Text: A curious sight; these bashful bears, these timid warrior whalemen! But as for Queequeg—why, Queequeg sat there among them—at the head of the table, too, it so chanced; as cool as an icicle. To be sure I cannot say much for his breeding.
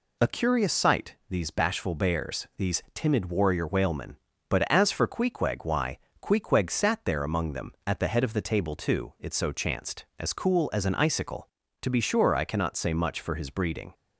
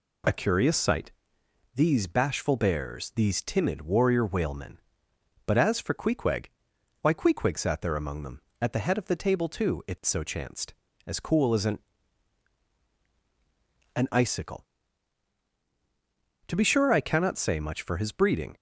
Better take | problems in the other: first | says "an" twice; at 13.9 s

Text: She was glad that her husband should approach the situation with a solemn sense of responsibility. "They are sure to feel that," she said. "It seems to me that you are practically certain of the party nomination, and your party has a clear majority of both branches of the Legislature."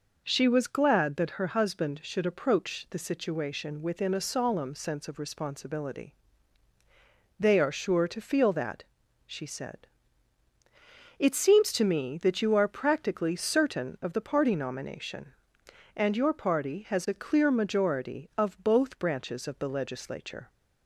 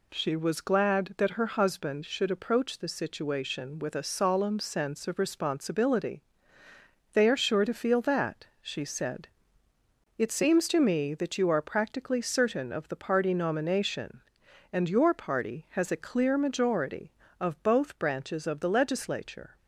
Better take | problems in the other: second | says "within" for "with"; at 3.8 s

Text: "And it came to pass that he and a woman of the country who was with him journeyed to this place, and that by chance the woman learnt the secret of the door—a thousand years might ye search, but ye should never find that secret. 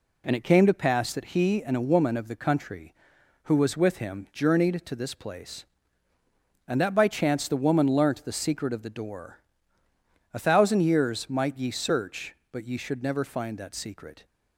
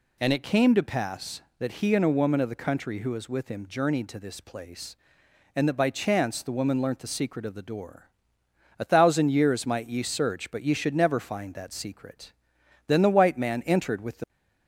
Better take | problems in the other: first | goes on to say "Then the white man entered with the"; from 12.8 s on; 1.4 s long

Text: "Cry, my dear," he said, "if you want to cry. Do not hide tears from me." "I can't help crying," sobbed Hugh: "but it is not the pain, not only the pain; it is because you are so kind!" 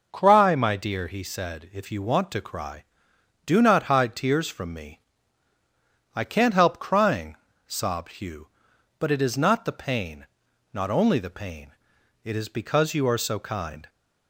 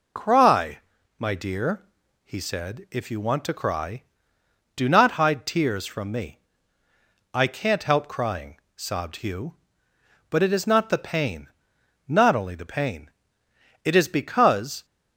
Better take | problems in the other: first | stops before "you are so kind"; at 14.8 s

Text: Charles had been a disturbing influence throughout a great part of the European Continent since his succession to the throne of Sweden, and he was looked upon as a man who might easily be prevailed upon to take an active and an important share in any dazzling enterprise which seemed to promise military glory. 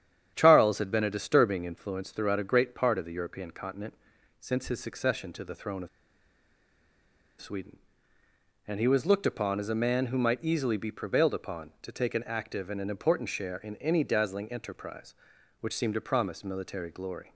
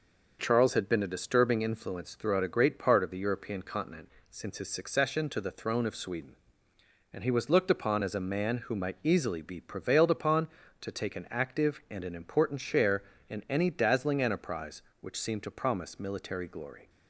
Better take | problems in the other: second | starts louder than the rest; strong; until 1.3 s; 9 dB // pauses between "Continent" and "since"; noticeable; at 3.9 s; 0.46 s long; slight in the second // pauses between "of" and "Sweden"; strong; at 5.8 s; 1.5 s long

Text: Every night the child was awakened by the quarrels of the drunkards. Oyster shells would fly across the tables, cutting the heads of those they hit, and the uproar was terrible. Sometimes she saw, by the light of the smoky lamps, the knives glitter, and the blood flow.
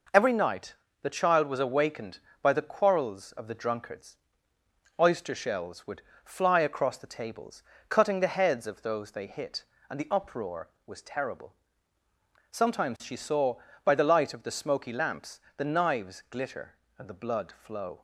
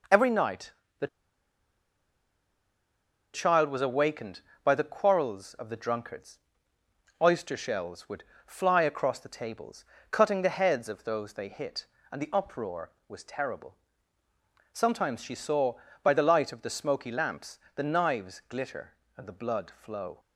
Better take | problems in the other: first | pauses between "night" and "the"; slight; at 0.7 s; 0.26 s long; slight in the first // pauses between "the" and "child"; strong; at 1.0 s; 2.2 s long // pauses between "would" and "fly"; slight; at 8.2 s; 0.22 s long; slight in the first

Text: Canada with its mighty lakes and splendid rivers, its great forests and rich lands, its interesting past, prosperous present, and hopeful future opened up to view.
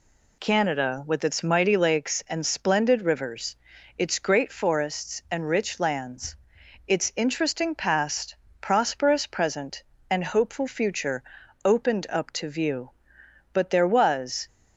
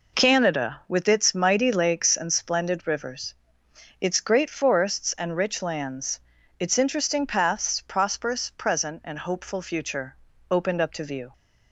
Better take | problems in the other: second | pauses between "future" and "opened"; at 11.2 s; 0.40 s long; slight in the second // goes on to say "But there was"; noticeable; from 13.5 s on; 0.94 s long

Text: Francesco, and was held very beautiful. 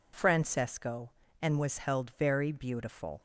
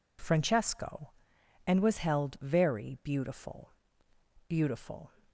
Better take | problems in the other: first | says "beautiful" twice; at 4.4 s

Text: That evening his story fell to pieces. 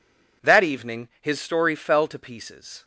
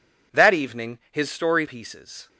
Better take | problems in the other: first | skips "fell to"; at 1.6 s

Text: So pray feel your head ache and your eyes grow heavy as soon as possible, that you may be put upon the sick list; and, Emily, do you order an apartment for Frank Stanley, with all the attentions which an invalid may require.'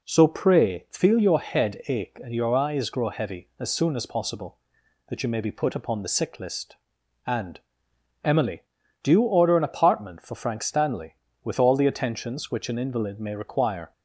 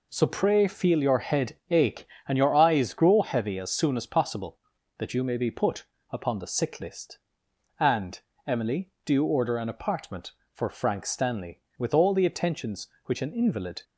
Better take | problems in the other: first | pauses between "put" and "upon"; slight; at 5.8 s; 0.24 s long // stops before "may require"; at 13.8 s

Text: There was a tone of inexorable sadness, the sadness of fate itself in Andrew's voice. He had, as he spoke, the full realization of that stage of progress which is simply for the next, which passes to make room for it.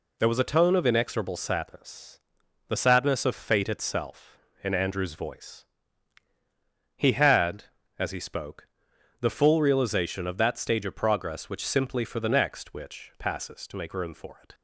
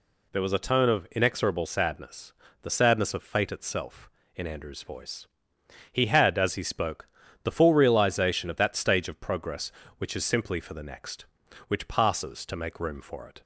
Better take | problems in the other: second | skips "is"; at 11.6 s

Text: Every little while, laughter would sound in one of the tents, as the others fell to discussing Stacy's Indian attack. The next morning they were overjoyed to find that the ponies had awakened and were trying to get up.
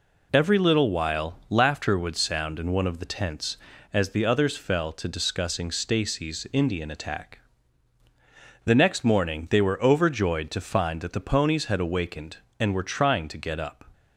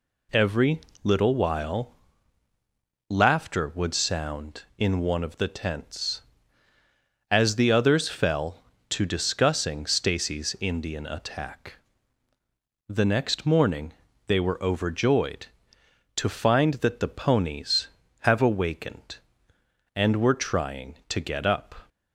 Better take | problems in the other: first | pauses between "Every" and "little"; slight; at 0.8 s; 0.22 s long // pauses between "morning" and "they"; slight; at 13.9 s; 0.36 s long // says "have" for "had"; at 18.2 s

